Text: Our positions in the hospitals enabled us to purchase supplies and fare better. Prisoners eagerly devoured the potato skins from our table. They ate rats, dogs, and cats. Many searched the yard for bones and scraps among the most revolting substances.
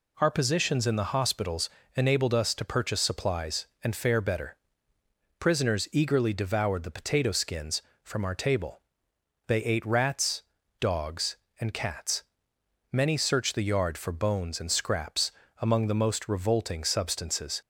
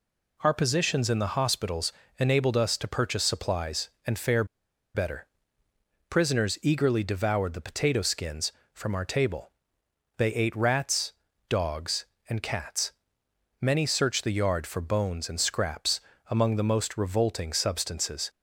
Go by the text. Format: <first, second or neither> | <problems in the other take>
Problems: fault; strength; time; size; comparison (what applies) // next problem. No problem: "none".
first | pauses between "hospitals" and "enabled"; slight; at 1.9 s; 0.26 s long; slight in the first // pauses between "fare" and "better"; noticeable; at 4.4 s; 0.50 s long // pauses between "scraps" and "among"; slight; at 15.9 s; 0.30 s long; slight in the first